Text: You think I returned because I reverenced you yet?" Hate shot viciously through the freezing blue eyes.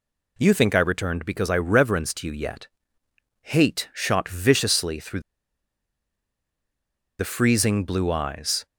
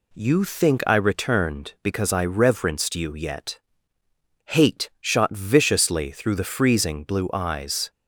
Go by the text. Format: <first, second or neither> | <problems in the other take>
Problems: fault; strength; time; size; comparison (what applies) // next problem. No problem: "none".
second | pauses between "through" and "the"; strong; at 5.2 s; 1.9 s long